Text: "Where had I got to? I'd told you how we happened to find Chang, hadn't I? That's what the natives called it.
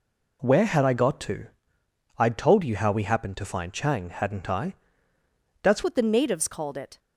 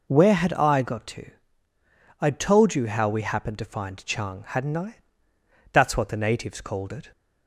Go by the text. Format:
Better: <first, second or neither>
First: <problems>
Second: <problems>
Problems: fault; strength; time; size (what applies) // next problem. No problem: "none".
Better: second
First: changes voice at "what"; from 5.8 s on; 1.1 s long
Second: none